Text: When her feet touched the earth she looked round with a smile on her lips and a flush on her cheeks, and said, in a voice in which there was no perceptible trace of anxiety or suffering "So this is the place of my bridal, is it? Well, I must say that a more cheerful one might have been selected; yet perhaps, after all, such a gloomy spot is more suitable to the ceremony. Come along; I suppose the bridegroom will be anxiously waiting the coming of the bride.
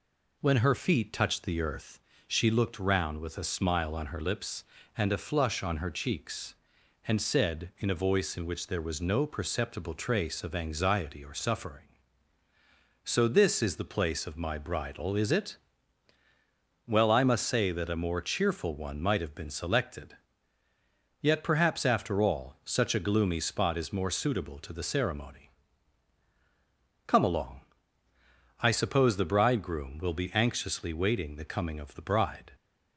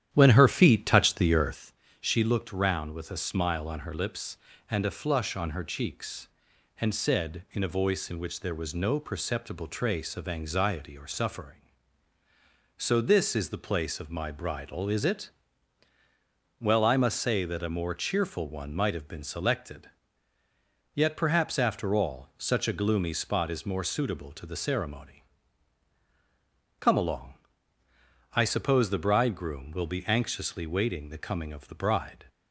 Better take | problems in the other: first | starts louder than the rest; strong; until 1.7 s; 11 dB // pauses between "earth" and "she"; slight; at 1.7 s; 0.28 s long; slight in the first

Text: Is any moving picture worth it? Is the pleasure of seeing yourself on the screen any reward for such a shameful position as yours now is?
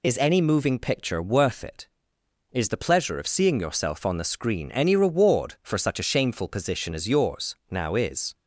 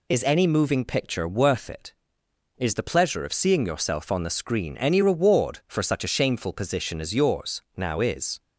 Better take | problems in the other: neither | none

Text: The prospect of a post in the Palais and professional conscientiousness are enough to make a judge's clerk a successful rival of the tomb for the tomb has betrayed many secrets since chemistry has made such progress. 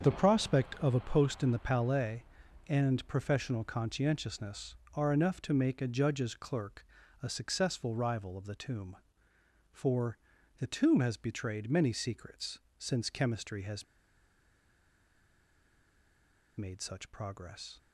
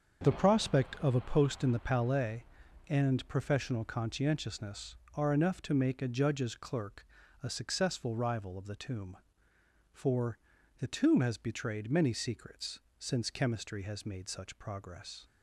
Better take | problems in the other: second | starts louder than the rest; until 1.1 s; 6.5 dB; also in the second // pauses between "clerk" and "a"; at 6.8 s; 0.38 s long; also in the second // pauses between "for" and "the"; at 10.1 s; 0.40 s long; also in the second // pauses between "secrets" and "since"; slight; at 12.5 s; 0.22 s long; slight in the second // pauses between "has" and "made"; strong; at 13.8 s; 2.7 s long

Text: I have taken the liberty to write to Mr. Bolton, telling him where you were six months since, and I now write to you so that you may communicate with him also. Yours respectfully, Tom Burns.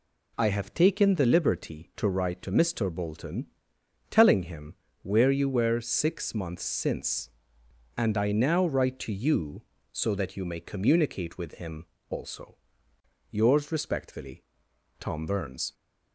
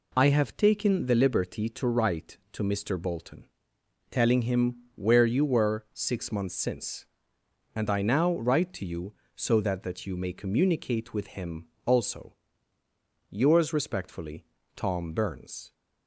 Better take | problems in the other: first | pauses between "him" and "where"; slight; at 4.7 s; 0.20 s long; slight in the first // says "that" twice; at 9.8 s // pauses between "him" and "also"; slight; at 11.6 s; 0.22 s long; slight in the first

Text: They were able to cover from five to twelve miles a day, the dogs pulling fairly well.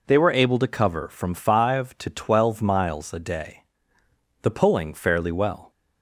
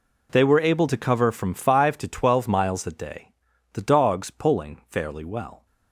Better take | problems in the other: second | skips "dogs"; at 4.5 s

